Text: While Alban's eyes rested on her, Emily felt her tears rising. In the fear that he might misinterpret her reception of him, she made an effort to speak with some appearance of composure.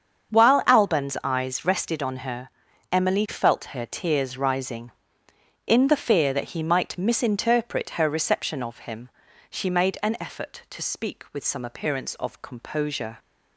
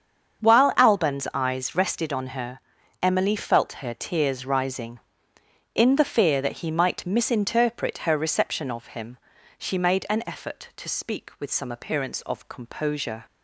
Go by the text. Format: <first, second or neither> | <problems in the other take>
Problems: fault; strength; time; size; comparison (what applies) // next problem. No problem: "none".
neither | starts louder than the rest; strong; the same in both